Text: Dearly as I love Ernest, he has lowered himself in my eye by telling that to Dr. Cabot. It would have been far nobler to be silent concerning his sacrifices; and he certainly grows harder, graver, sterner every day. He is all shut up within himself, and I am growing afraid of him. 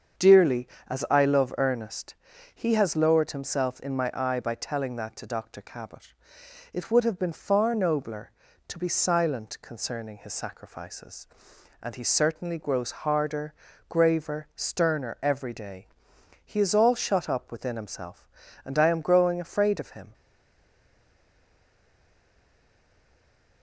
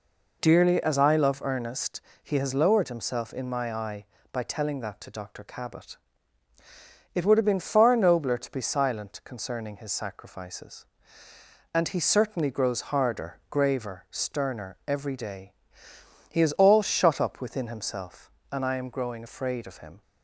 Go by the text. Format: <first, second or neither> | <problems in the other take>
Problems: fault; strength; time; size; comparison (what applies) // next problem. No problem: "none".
second | starts louder than the rest; strong; until 1.4 s; 7 dB // stays silent after the last word; strong; from 20.1 s on; 3.5 s long